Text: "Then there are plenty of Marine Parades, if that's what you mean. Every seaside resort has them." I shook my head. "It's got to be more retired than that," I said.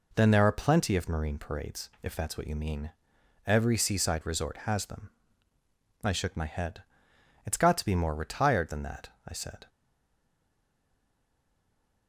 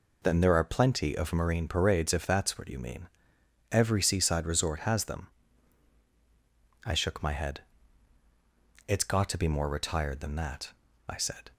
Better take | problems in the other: second | stays silent after the last word; from 9.6 s on; 2.4 s long

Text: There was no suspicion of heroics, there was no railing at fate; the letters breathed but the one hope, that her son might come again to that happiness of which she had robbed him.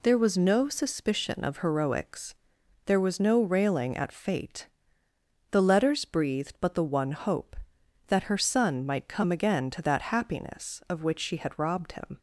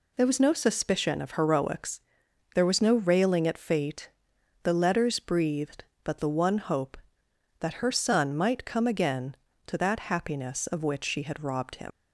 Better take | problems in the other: first | leaves "him" unfinished; at 11.9 s; 100 ms

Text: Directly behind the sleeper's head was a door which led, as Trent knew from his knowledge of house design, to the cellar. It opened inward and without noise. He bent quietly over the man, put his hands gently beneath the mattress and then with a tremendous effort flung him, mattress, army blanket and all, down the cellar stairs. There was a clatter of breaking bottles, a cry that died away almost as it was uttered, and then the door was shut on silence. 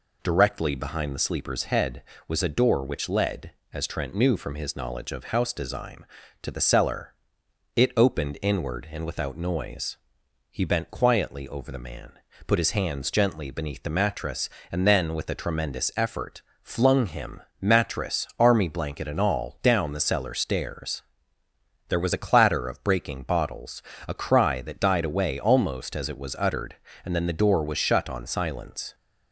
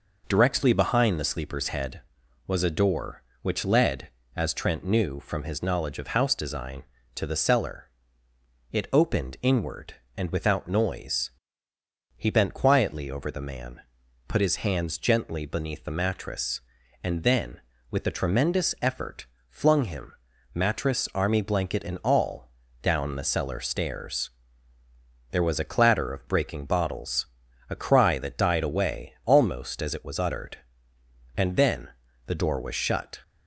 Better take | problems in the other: first | pauses between "effort" and "flung"; slight; at 19.2 s; 0.24 s long; slight in the first // pauses between "then" and "the"; at 31.8 s; 0.38 s long // stops before "on silence"; at 33.2 s

